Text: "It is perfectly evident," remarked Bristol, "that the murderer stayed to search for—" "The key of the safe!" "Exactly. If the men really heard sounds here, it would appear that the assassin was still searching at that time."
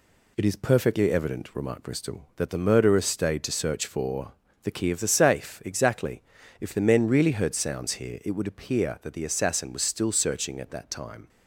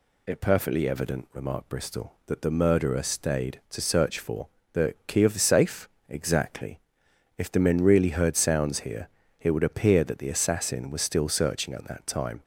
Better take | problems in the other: first | skips "is"; at 0.3 s

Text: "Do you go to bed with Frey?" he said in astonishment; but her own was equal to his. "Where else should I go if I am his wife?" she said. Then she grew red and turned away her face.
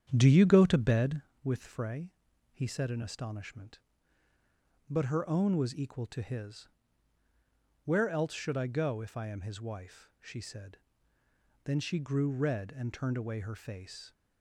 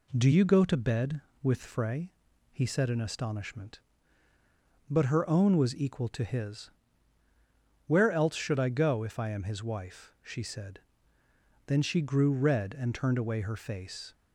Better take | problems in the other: second | starts louder than the rest; strong; until 1.4 s; 8.5 dB

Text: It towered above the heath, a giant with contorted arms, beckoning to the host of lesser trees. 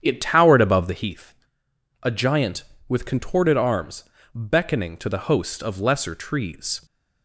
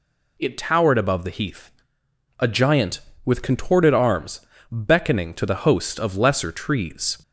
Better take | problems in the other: second | starts louder than the rest; strong; until 1.1 s; 8.5 dB

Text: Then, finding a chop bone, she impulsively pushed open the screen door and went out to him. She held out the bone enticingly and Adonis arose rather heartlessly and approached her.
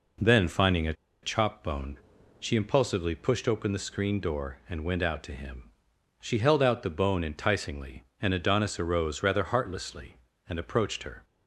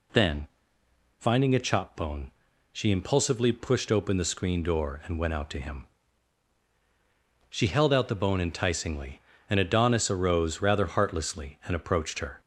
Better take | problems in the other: second | pauses between "a" and "chop"; slight; at 0.9 s; 0.29 s long

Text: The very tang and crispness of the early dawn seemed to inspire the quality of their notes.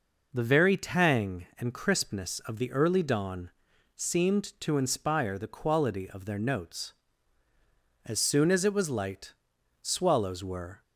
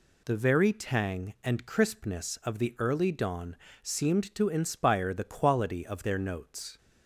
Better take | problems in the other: second | pauses between "dawn" and "seemed"; noticeable; at 3.4 s; 0.48 s long; slight in the second // goes on to say "As soon as it was light Swallows were"; strong; from 8.0 s on; 2.7 s long

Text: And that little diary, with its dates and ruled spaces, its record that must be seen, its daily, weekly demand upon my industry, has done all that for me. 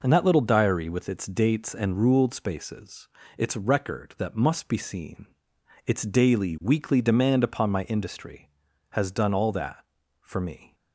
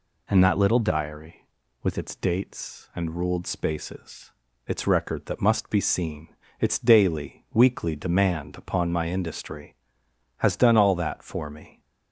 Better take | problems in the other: neither | none

